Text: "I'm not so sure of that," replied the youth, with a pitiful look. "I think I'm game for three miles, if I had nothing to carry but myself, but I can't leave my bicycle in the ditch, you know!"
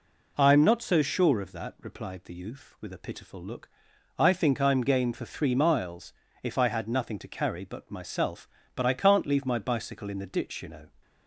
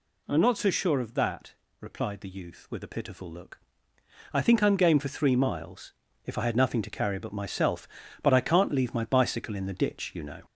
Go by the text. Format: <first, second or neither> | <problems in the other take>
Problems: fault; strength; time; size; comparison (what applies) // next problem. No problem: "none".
first | gets louder; slight; throughout; 3.5 dB